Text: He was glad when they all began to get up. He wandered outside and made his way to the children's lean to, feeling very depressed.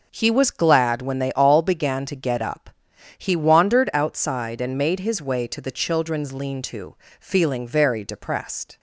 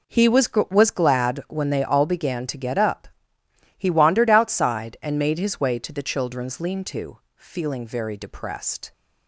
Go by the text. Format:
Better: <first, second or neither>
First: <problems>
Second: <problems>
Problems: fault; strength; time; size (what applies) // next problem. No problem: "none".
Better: first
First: none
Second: says "was" twice; at 0.7 s